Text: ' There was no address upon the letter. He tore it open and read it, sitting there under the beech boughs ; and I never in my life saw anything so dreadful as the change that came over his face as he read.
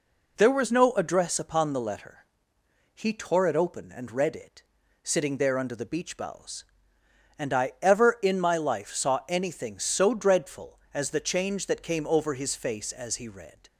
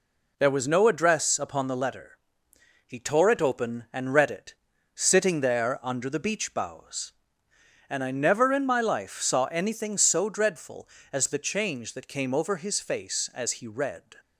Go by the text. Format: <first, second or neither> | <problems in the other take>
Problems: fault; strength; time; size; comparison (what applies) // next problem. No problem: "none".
second | says "ever" for "never"; at 7.8 s